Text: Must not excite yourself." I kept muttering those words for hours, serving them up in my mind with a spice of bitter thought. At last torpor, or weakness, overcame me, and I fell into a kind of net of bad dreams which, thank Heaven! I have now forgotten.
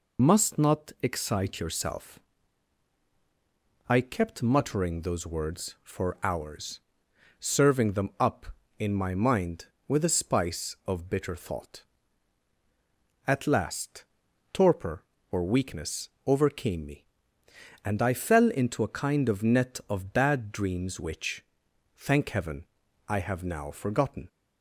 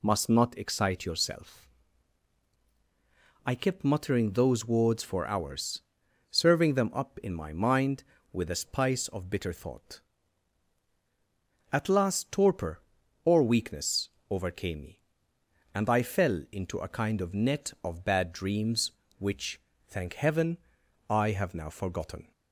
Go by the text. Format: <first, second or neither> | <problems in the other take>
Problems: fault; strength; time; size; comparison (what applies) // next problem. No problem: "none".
second | loses the start of "Must"; at 0.1 s; 60 ms // pauses between "last" and "torpor"; noticeable; at 14.0 s; 0.48 s long